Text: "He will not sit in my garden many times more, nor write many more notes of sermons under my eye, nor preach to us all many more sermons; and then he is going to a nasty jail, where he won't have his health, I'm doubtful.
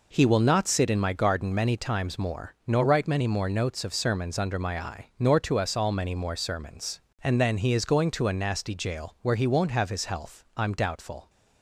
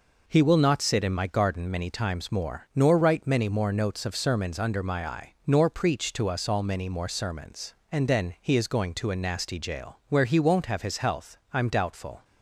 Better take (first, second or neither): second